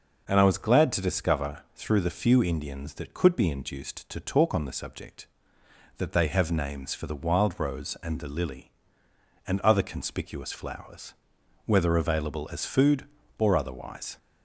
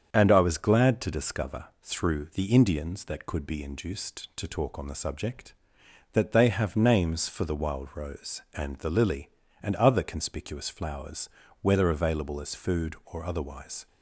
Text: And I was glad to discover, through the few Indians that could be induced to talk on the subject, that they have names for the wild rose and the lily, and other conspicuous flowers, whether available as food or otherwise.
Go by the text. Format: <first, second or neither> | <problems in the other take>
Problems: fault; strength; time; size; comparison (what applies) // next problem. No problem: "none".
first | starts louder than the rest; strong; until 1.1 s; 7.5 dB // skips "few"; at 2.4 s